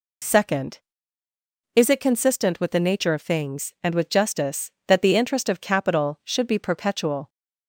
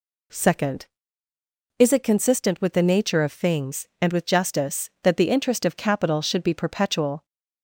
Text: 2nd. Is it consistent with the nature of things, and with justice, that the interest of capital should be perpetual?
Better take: neither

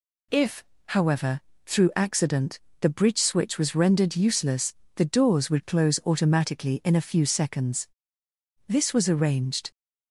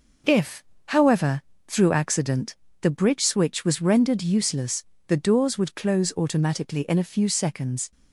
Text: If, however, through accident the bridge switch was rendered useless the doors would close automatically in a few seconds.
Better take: second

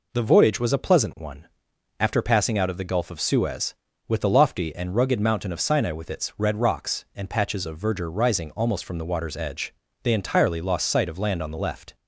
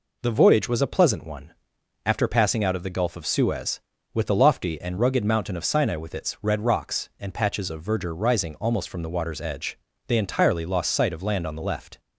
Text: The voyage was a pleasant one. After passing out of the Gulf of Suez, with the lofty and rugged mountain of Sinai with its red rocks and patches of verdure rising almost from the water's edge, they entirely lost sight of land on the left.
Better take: neither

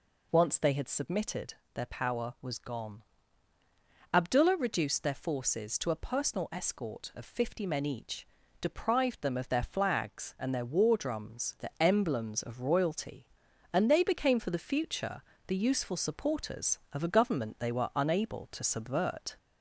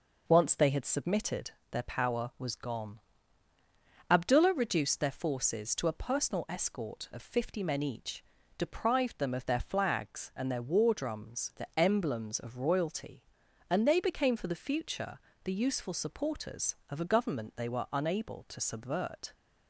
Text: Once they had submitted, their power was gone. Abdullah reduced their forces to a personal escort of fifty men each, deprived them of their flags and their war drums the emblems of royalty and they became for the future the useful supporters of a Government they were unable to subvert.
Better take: second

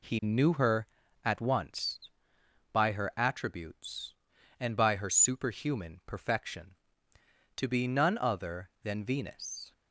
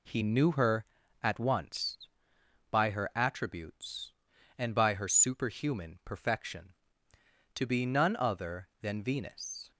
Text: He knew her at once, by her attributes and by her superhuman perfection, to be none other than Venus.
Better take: neither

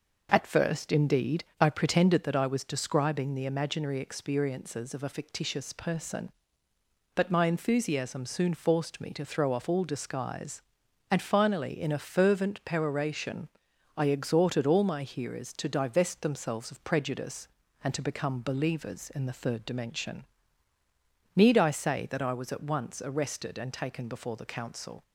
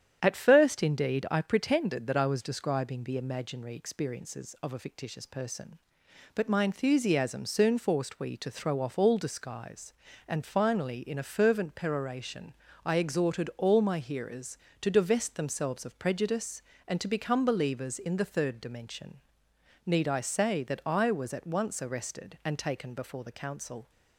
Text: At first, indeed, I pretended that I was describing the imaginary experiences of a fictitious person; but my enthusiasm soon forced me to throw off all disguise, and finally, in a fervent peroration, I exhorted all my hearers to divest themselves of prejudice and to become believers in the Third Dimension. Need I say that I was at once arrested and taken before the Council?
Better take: first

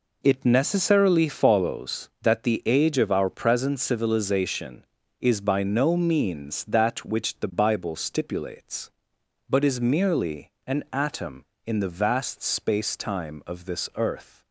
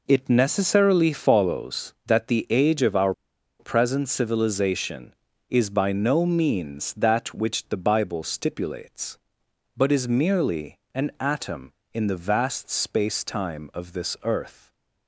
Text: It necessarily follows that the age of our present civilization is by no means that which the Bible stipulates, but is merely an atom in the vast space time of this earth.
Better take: first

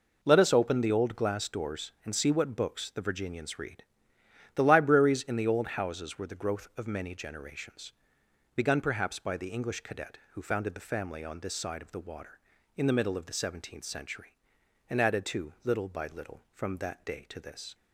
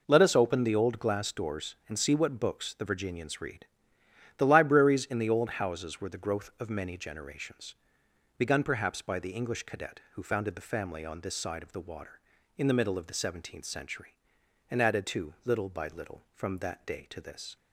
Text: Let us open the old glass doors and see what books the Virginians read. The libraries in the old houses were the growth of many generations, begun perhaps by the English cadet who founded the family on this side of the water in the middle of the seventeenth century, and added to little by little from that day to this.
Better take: neither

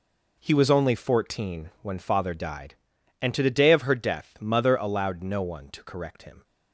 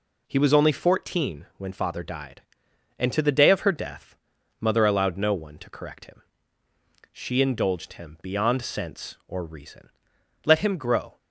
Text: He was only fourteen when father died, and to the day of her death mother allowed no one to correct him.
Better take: first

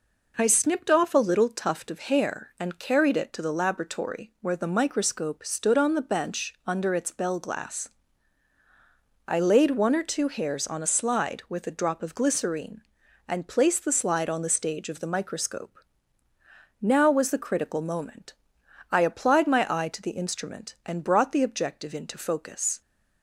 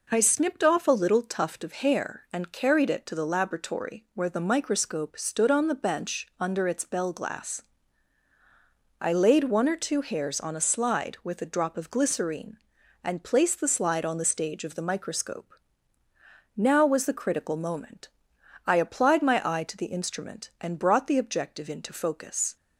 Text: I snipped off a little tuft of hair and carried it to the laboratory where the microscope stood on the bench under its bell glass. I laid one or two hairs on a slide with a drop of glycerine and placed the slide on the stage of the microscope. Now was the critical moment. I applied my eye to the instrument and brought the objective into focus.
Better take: neither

